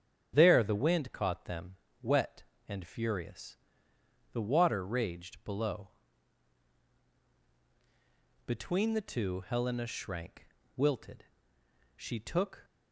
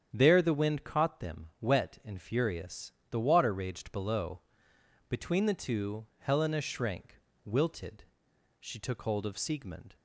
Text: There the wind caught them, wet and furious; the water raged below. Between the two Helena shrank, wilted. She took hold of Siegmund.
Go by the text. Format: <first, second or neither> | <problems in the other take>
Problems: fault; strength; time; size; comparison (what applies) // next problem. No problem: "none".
second | starts louder than the rest; strong; until 1.3 s; 9 dB; strong in the second // stops before "hold of Siegmund"; at 12.6 s